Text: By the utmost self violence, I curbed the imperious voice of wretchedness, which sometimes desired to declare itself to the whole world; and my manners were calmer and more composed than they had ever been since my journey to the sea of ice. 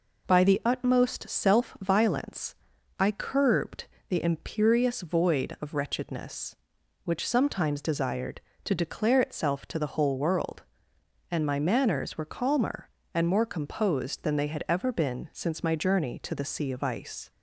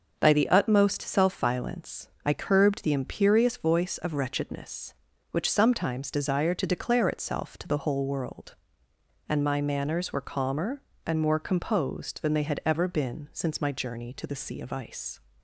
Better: second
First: pauses between "curbed" and "the"; slight; at 3.8 s; 0.22 s long // says "void" for "voice"; at 5.0 s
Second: none

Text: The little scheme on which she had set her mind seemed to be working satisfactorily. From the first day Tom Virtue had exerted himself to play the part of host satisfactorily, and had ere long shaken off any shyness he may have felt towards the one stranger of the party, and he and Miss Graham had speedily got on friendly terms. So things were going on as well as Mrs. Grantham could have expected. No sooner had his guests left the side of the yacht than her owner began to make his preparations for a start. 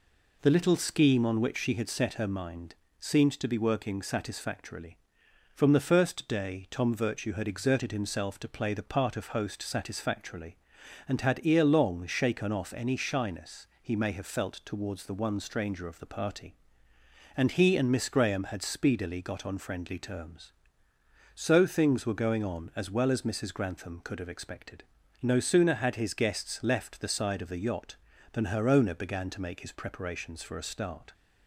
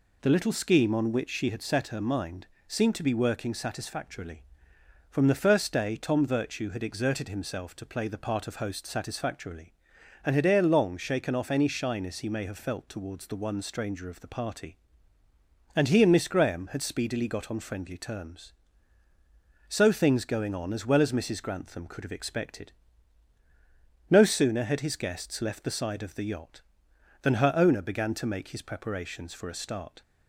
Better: first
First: pauses between "mind" and "seemed"; slight; at 2.7 s; 0.26 s long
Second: pauses between "mind" and "seemed"; slight; at 2.4 s; 0.20 s long // skips "were"; at 20.2 s

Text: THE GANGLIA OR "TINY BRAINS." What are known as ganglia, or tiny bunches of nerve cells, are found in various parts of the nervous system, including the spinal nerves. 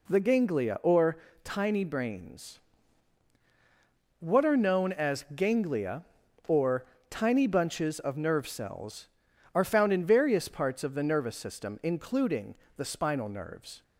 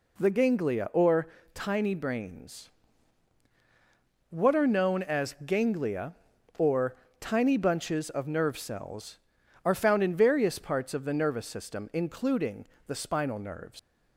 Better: first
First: pauses between "OR" and "TINY"; slight; at 1.1 s; 0.26 s long // pauses between "or" and "tiny"; slight; at 6.8 s; 0.26 s long // pauses between "including" and "the"; slight; at 12.5 s; 0.22 s long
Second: pauses between "OR" and "TINY"; slight; at 1.2 s; 0.26 s long // pauses between "or" and "tiny"; slight; at 6.9 s; 0.26 s long // pauses between "including" and "the"; slight; at 12.6 s; 0.22 s long // leaves "nerves" unfinished; at 13.7 s; 130 ms

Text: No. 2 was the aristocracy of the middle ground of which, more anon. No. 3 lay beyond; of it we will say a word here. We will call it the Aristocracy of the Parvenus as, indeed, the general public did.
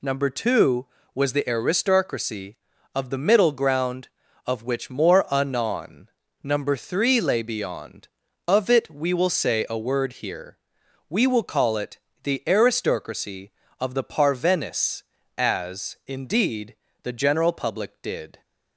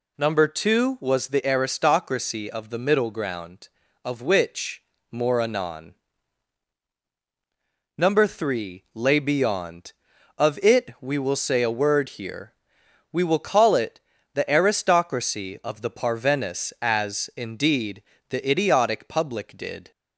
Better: first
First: pauses between "it" and "the"; slight; at 11.9 s; 0.24 s long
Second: pauses between "it" and "the"; slight; at 13.9 s; 0.36 s long // says "idiotic" for "general"; at 18.4 s

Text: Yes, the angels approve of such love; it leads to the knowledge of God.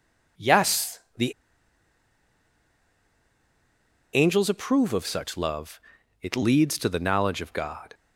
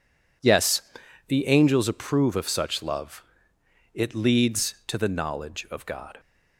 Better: second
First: pauses between "the" and "angels"; strong; at 1.3 s; 2.8 s long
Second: none

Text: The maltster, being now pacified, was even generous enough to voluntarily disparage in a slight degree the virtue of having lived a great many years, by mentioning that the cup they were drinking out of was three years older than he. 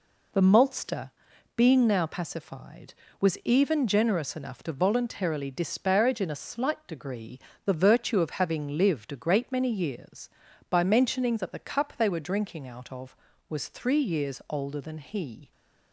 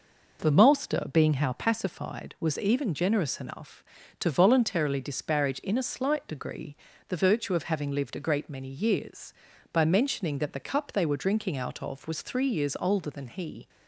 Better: first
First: pauses between "degree" and "the"; slight; at 7.3 s; 0.28 s long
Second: says "how" for "now"; at 1.3 s // pauses between "degree" and "the"; slight; at 6.7 s; 0.32 s long

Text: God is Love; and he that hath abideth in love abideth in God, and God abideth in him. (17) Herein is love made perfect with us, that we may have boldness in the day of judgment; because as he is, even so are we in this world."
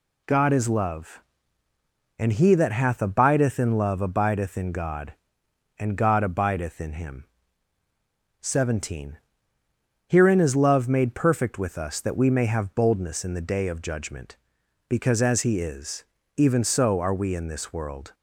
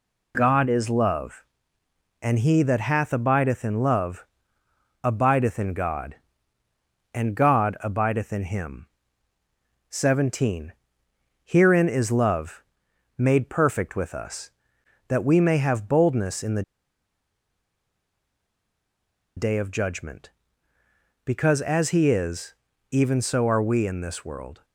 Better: first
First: none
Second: pauses between "love" and "abideth"; noticeable; at 4.2 s; 0.76 s long // pauses between "love" and "made"; noticeable; at 12.6 s; 0.54 s long // pauses between "the" and "day"; strong; at 16.6 s; 2.7 s long

